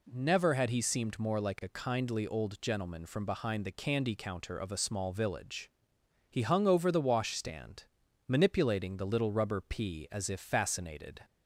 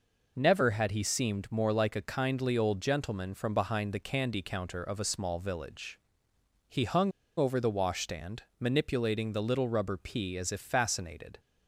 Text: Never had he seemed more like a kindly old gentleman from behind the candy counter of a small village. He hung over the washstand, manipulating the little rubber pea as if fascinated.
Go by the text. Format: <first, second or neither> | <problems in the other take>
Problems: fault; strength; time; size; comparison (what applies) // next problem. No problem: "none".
first | pauses between "hung" and "over"; slight; at 7.1 s; 0.26 s long